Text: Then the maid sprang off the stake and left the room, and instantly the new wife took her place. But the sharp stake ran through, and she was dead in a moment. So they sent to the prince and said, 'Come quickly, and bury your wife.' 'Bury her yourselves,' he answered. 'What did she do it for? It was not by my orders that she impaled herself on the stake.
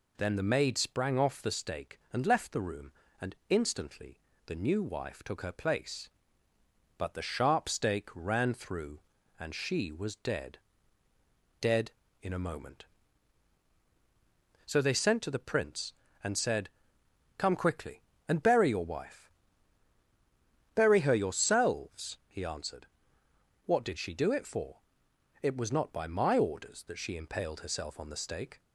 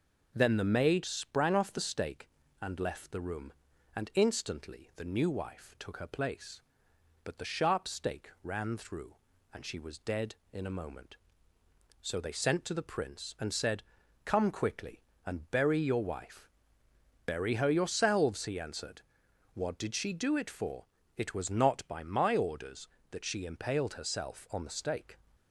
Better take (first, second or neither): second